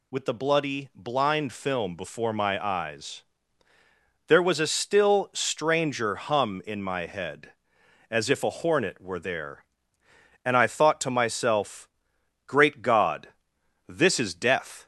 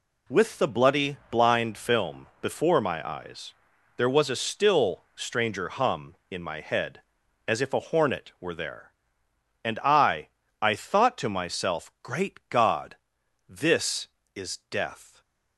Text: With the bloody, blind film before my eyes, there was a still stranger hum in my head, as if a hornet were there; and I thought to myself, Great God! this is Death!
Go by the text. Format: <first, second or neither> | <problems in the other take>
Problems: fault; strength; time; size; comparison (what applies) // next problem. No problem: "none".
first | says "I" twice; at 10.6 s